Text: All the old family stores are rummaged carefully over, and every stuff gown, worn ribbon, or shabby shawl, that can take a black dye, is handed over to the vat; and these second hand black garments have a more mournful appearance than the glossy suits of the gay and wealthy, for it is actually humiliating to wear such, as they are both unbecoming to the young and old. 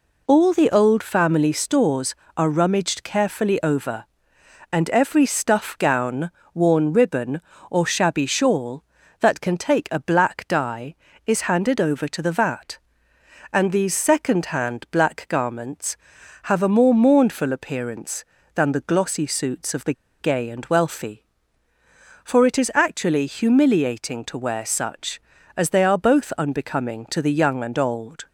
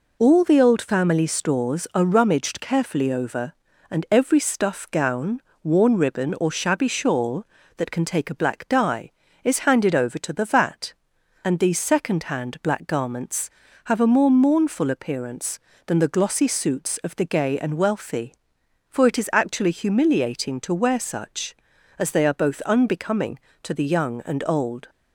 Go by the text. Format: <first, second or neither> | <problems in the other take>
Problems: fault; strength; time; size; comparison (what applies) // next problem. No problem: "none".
second | pauses between "the" and "gay"; slight; at 19.9 s; 0.27 s long